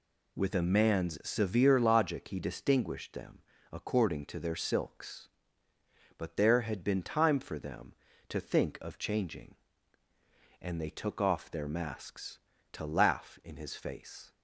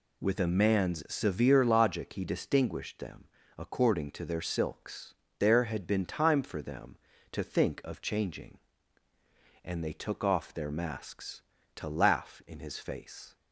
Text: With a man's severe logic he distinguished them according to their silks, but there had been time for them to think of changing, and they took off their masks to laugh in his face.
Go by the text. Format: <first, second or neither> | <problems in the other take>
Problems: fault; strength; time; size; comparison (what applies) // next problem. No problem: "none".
first | pauses between "them" and "according"; slight; at 3.2 s; 0.32 s long; slight in the first // skips "but"; at 5.2 s